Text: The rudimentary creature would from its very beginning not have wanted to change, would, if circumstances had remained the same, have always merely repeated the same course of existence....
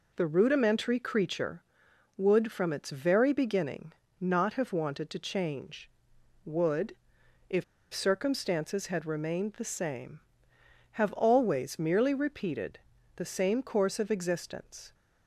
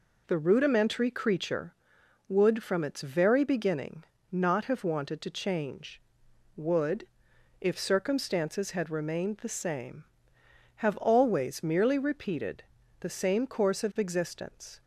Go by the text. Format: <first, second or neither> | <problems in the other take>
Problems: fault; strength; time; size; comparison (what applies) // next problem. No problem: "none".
second | pauses between "beginning" and "not"; slight; at 3.9 s; 0.28 s long; slight in the second // pauses between "if" and "circumstances"; slight; at 7.6 s; 0.29 s long // pauses between "repeated" and "the"; slight; at 12.7 s; 0.36 s long; slight in the second